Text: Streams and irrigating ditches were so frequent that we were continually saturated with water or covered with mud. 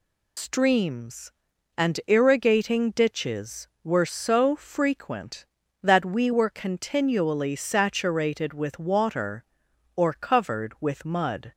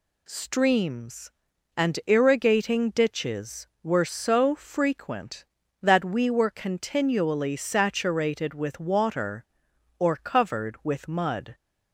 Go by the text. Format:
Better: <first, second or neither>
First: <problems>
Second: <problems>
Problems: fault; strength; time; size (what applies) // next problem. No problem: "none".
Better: second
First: loses the start of "Streams"; at 0.3 s; 80 ms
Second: none